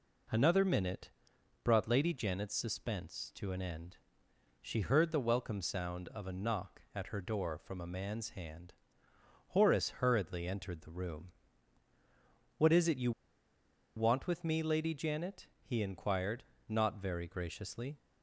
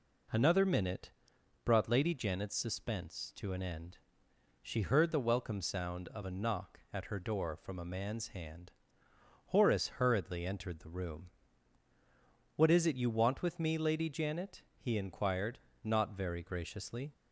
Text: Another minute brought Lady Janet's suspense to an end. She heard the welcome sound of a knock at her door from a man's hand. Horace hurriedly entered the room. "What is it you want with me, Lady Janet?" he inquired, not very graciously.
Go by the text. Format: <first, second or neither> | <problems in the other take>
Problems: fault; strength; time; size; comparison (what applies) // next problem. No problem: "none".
second | pauses between "minute" and "brought"; noticeable; at 1.0 s; 0.56 s long; noticeable in the second // pauses between "you" and "want"; noticeable; at 13.1 s; 0.85 s long